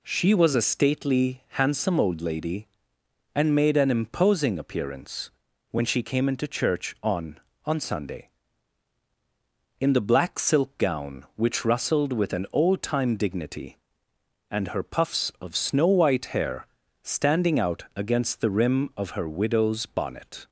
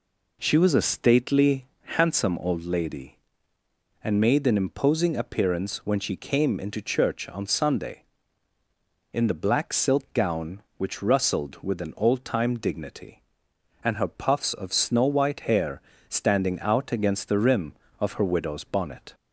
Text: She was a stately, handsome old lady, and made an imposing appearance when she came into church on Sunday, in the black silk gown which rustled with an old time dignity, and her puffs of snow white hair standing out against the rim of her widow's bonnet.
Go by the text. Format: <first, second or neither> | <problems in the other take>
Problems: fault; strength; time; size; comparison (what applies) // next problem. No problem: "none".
second | pauses between "appearance" and "when"; at 5.3 s; 0.40 s long // says "on" twice; at 7.6 s // pauses between "hair" and "standing"; at 16.6 s; 0.38 s long; slight in the second